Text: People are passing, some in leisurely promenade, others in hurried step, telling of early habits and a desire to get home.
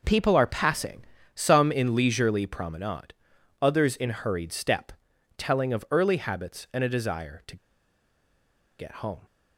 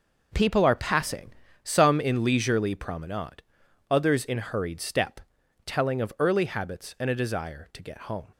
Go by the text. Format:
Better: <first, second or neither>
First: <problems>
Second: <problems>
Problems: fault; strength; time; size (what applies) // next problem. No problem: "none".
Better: second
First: pauses between "to" and "get"; at 7.5 s; 1.2 s long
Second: none